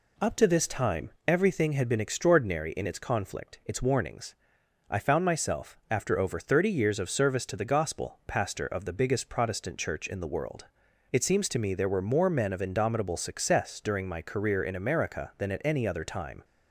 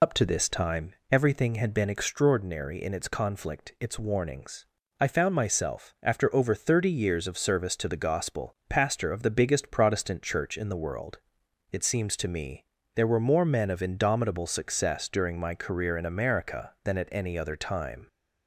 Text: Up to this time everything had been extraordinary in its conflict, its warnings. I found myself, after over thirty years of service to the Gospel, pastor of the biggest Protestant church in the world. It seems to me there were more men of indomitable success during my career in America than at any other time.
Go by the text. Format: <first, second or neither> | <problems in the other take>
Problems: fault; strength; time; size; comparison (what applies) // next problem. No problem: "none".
first | loses the start of "Up"; at 0.0 s; 65 ms // pauses between "time" and "everything"; slight; at 0.9 s; 0.18 s long; slight in the first // pauses between "me" and "there"; slight; at 12.6 s; 0.30 s long